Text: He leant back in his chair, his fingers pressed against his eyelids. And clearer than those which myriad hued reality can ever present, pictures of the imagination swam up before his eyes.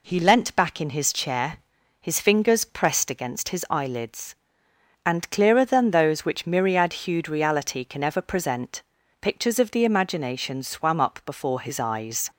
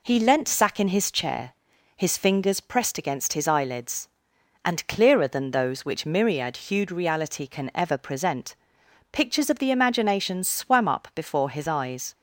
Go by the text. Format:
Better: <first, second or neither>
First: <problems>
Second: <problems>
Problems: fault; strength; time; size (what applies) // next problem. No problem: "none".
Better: first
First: none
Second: says "sack" for "back"; at 0.4 s